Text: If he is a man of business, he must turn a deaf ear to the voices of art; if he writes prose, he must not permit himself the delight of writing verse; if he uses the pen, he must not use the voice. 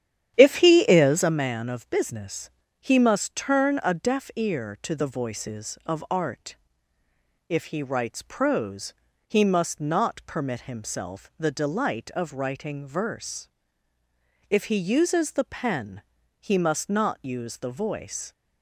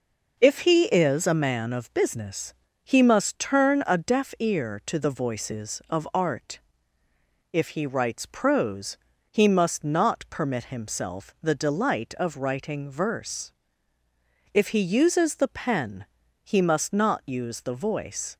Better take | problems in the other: second | starts louder than the rest; strong; until 1.3 s; 10 dB

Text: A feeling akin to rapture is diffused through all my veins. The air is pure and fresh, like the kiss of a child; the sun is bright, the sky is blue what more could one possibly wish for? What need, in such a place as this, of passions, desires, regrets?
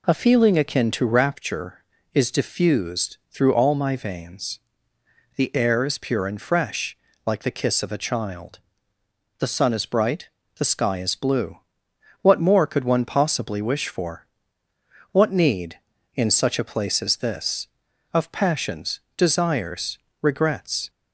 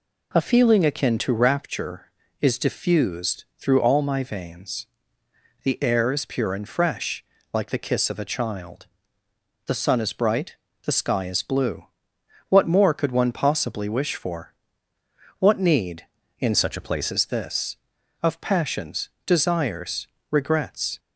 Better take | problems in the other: first | pauses between "blue" and "what"; noticeable; at 11.8 s; 0.64 s long; noticeable in the first // changes voice from "such" to "place"; from 16.5 to 17.1 s; 0.6 s long

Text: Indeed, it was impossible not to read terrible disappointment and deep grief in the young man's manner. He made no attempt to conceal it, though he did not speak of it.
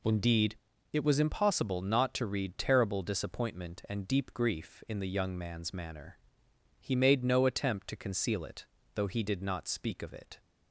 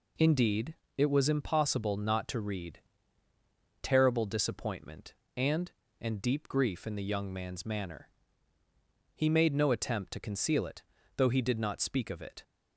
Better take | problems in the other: first | pauses between "read" and "terrible"; at 2.7 s; 1.0 s long // says "and" twice; at 6.0 s

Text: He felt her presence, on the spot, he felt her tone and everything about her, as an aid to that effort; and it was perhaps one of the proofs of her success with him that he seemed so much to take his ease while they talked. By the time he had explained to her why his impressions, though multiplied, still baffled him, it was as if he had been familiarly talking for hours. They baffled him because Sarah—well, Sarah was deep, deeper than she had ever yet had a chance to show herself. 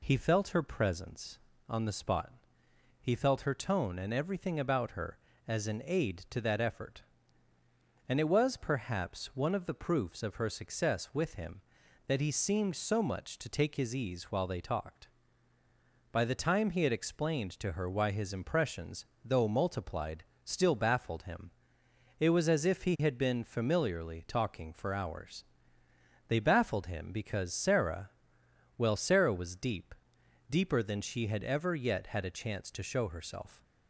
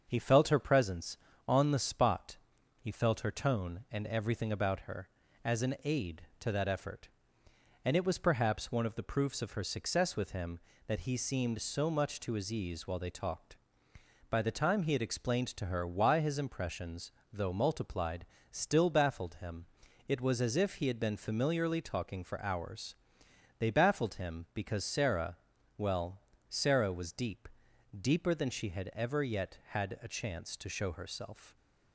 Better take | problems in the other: first | starts louder than the rest; until 1.0 s; 7 dB // skips "take"; at 12.3 s

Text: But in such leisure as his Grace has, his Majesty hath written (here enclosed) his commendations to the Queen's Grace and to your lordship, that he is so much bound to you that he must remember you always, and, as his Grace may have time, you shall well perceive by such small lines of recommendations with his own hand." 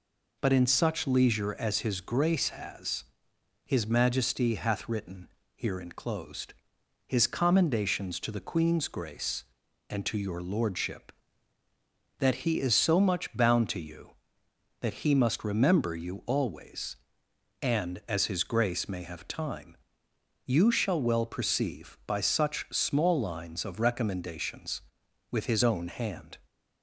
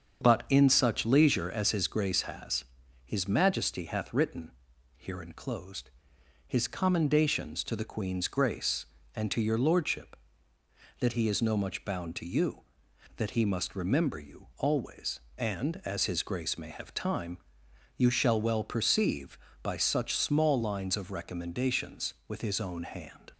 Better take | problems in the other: first | starts louder than the rest; until 1.2 s; 7 dB // says "no" for "so"; at 11.4 s

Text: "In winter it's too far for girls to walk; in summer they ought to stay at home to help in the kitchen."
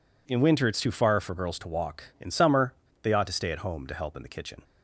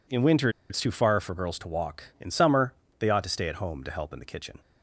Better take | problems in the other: first | pauses between "winter" and "it's"; slight; at 0.4 s; 0.20 s long // pauses between "summer" and "they"; slight; at 2.7 s; 0.24 s long; slight in the first

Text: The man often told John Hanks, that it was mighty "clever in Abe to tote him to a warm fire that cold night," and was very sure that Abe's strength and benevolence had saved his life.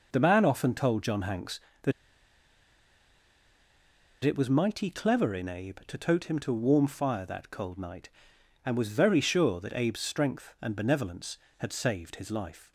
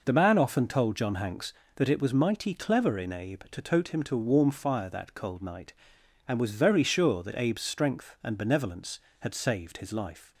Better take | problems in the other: second | pauses between "that" and "it"; strong; at 1.9 s; 2.3 s long

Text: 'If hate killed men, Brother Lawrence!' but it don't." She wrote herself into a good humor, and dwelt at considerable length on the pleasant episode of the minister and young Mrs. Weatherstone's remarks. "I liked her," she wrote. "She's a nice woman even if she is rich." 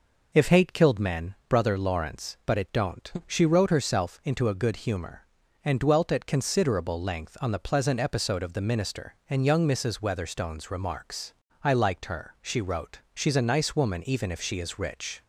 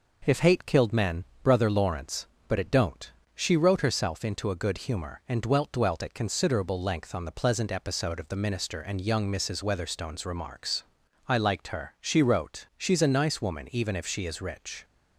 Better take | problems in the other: first | says "dwelt" twice; at 5.7 s

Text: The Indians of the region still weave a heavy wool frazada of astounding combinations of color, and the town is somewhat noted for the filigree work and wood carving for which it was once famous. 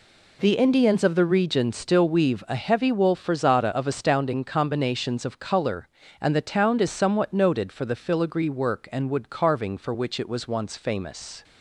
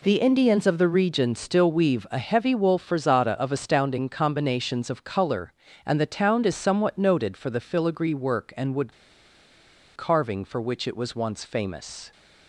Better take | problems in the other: first | pauses between "wood" and "carving"; at 8.9 s; 1.0 s long

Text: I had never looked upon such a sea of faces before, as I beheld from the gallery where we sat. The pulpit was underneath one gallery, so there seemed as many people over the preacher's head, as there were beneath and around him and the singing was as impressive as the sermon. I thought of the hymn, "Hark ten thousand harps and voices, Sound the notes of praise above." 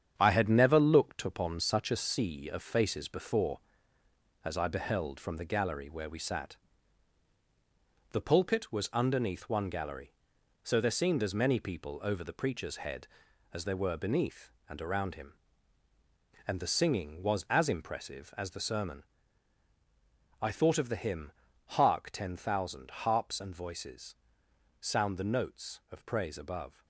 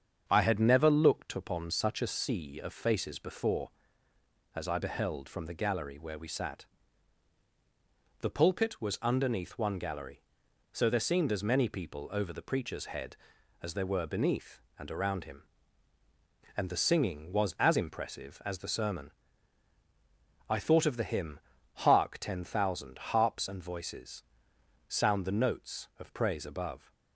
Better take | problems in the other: second | gets quieter; throughout; 6 dB // starts louder than the rest; strong; until 1.1 s; 8.5 dB; strong in the second

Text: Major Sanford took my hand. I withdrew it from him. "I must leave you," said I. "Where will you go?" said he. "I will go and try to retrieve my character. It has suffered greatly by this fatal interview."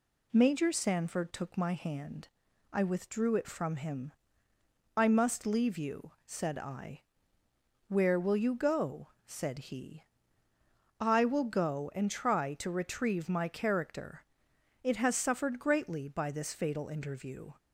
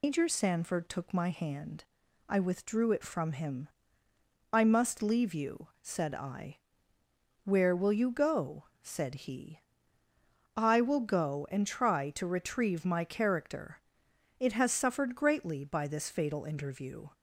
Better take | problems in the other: first | loses the start of "Major"; at 0.0 s; 155 ms

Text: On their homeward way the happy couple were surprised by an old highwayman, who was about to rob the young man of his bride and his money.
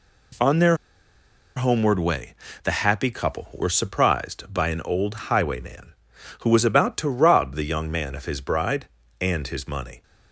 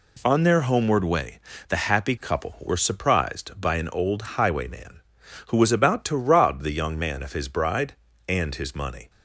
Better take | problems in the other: second | pauses between "their" and "homeward"; noticeable; at 0.7 s; 0.79 s long // pauses between "way" and "the"; slight; at 2.3 s; 0.30 s long; slight in the second

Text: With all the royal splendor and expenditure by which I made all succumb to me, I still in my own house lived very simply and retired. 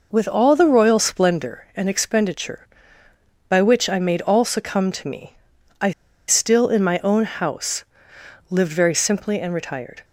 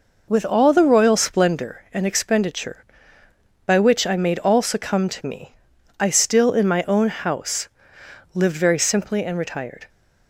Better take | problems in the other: second | pauses between "I" and "still"; at 5.9 s; 0.36 s long // pauses between "house" and "lived"; noticeable; at 7.8 s; 0.64 s long; noticeable in the second

